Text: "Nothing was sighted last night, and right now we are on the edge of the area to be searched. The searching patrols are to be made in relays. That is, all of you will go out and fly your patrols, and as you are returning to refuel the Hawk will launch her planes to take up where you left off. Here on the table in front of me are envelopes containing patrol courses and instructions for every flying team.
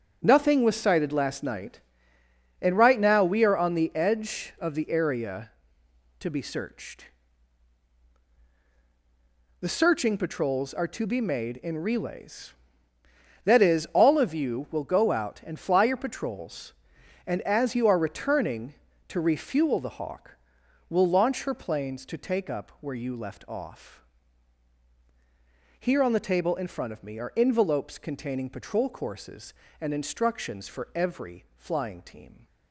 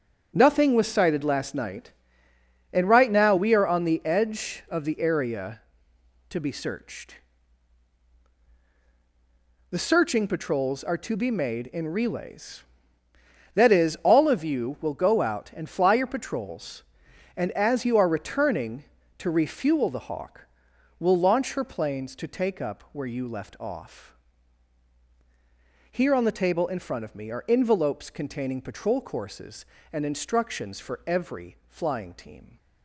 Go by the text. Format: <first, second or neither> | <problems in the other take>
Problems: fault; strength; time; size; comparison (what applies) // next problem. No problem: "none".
neither | starts louder than the rest; strong; the same in both